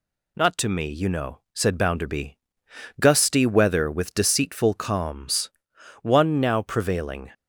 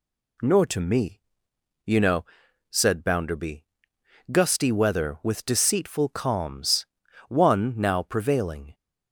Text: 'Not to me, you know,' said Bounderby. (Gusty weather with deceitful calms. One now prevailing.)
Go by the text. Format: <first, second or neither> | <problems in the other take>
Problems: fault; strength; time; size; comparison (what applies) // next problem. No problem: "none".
first | says "Nor" for "Not"; at 0.4 s